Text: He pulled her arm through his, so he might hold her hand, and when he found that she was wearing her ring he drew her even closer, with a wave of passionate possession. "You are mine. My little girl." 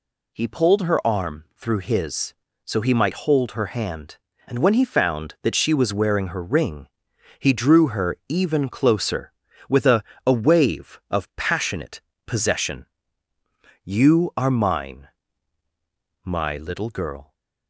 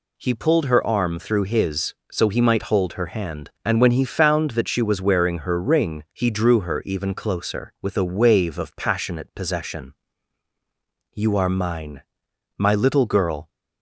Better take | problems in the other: second | pauses between "ring" and "he"; noticeable; at 6.8 s; 0.52 s long // says "a" twice; at 10.2 s // pauses between "passionate" and "possession"; slight; at 11.9 s; 0.26 s long

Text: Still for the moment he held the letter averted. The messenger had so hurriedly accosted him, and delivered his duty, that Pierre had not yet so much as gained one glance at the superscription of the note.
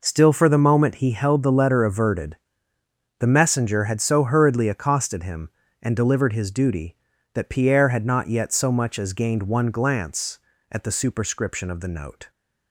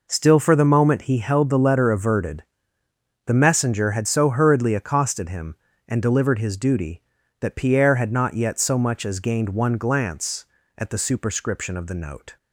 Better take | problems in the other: neither | none

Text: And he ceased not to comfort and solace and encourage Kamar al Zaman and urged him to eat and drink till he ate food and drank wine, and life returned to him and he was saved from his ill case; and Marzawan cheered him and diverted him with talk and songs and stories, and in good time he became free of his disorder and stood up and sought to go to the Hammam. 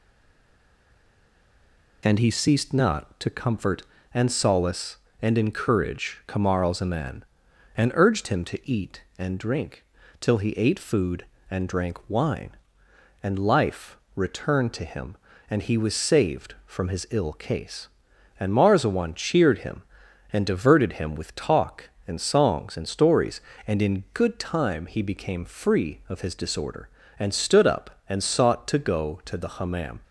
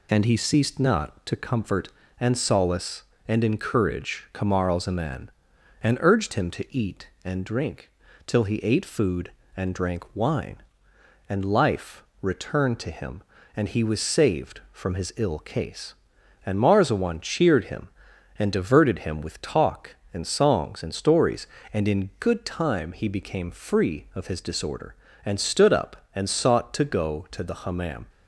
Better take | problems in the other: second | stays silent before the first word; noticeable; until 2.0 s; 2.0 s long // pauses between "drink" and "till"; slight; at 9.8 s; 0.36 s long; slight in the second // pauses between "life" and "returned"; slight; at 13.9 s; 0.20 s long; slight in the second

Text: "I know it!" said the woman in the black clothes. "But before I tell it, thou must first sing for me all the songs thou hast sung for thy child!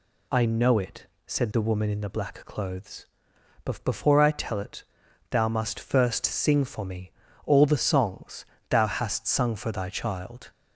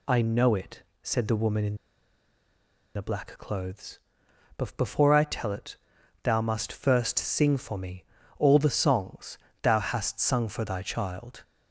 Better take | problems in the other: first | pauses between "in" and "the"; at 1.7 s; 1.1 s long // pauses between "me" and "all"; slight; at 8.0 s; 0.34 s long; slight in the first // pauses between "songs" and "thou"; slight; at 9.3 s; 0.24 s long; slight in the first

